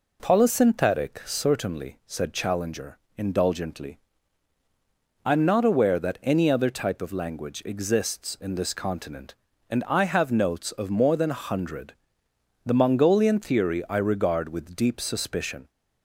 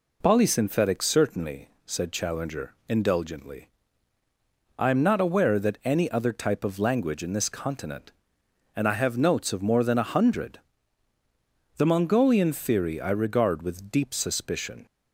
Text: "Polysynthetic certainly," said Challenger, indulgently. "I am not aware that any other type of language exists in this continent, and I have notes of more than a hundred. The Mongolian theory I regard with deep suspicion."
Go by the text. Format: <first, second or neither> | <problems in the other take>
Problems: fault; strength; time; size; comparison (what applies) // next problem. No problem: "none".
first | skips "exists"; at 7.2 s